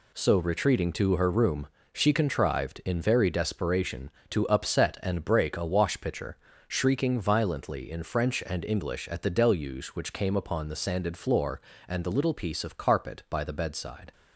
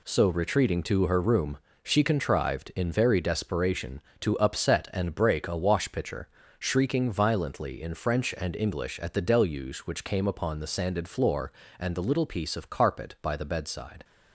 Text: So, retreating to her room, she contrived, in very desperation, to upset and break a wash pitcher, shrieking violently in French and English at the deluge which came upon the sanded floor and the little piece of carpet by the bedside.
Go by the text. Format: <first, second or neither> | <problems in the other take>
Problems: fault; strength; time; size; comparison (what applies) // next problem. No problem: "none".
neither | none